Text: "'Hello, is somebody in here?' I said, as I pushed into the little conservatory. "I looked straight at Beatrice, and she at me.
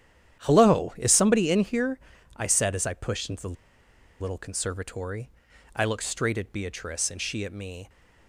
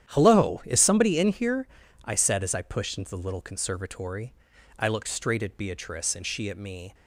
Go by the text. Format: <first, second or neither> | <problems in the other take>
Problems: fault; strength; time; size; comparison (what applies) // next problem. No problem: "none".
second | starts louder than the rest; strong; until 1.4 s; 10 dB; strong in the second // pauses between "the" and "little"; noticeable; at 3.5 s; 0.66 s long